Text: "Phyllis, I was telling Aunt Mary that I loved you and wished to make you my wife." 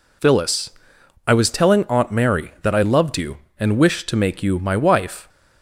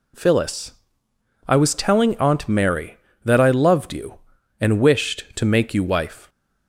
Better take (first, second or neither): first